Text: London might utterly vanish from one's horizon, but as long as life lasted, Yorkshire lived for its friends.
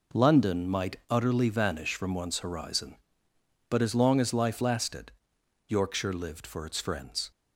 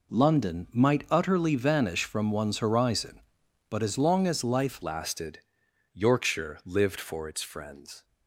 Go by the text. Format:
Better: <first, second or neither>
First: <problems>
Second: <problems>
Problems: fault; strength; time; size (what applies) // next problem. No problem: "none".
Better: first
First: none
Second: changes voice at "lasted"; from 4.8 s on; 3.2 s long